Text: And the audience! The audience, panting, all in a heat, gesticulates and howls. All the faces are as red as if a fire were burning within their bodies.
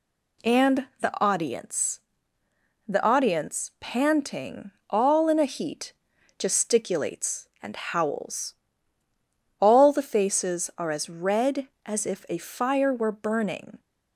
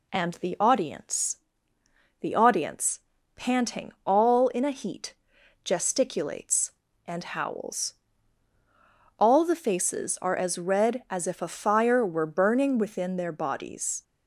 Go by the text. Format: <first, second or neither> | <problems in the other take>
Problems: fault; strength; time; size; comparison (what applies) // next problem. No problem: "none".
second | pauses between "And" and "the"; slight; at 0.8 s; 0.16 s long // stops before "within their bodies"; at 13.7 s